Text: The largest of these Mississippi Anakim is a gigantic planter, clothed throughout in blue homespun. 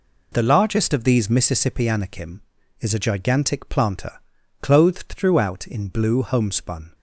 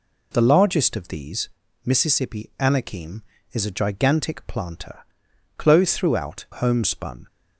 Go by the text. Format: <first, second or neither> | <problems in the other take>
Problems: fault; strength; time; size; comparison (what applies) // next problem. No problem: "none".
first | pauses between "these" and "Mississippi"; slight; at 1.5 s; 0.34 s long // skips "in blue"; at 6.4 s